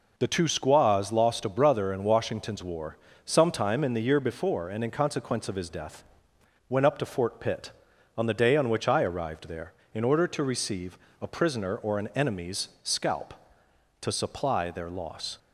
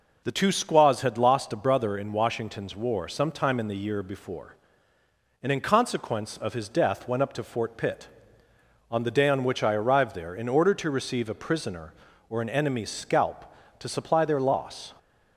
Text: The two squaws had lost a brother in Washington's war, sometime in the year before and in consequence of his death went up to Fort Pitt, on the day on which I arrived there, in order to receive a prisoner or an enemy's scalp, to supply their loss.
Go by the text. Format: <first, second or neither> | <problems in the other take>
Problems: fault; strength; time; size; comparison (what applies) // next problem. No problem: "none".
second | skips "had"; at 1.1 s // pauses between "death" and "went"; noticeable; at 6.0 s; 0.66 s long // pauses between "receive" and "a"; slight; at 10.9 s; 0.24 s long